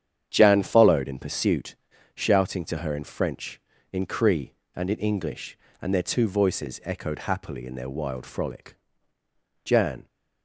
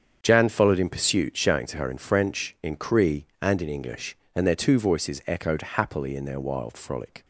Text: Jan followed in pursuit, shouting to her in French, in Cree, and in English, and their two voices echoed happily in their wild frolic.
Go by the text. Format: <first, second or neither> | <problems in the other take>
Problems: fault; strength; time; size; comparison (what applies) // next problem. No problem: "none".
second | starts louder than the rest; strong; until 1.3 s; 9 dB; strong in the second // goes on to say "Jan"; slight; from 9.6 s on; 0.44 s long